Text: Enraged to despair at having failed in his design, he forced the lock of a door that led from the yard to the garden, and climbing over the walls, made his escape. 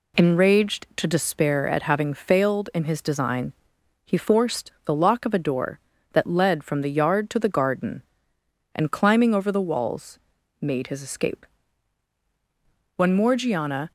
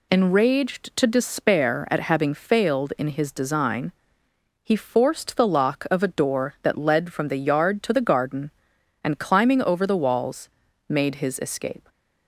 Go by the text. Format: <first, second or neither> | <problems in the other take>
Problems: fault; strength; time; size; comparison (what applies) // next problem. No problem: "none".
second | goes on to say "When Morgiana"; noticeable; from 12.9 s on; 0.96 s long